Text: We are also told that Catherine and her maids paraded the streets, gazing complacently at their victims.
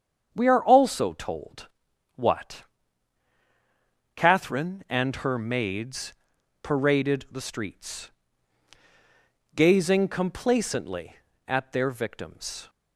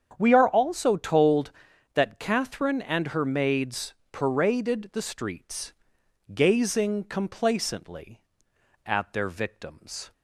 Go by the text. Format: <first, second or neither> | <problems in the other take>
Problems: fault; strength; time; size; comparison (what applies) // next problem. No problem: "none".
second | starts louder than the rest; strong; until 1.3 s; 7.5 dB; strong in the second // says "what" for "that"; at 2.1 s // pauses between "maids" and "paraded"; noticeable; at 6.1 s; 0.48 s long; slight in the second